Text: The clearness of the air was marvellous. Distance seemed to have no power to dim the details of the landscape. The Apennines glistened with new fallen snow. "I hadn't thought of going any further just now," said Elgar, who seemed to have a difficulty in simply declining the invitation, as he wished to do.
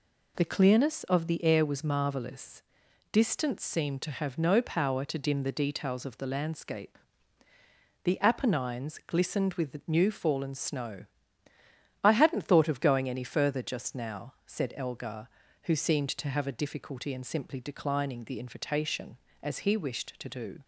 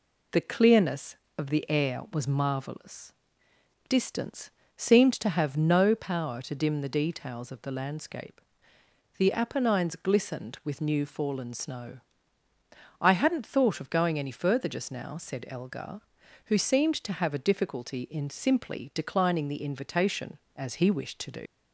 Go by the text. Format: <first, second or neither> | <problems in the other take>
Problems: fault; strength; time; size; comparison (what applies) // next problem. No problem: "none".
first | pauses between "Distance" and "seemed"; slight; at 4.5 s; 0.24 s long // leaves "do" unfinished; at 21.4 s; 100 ms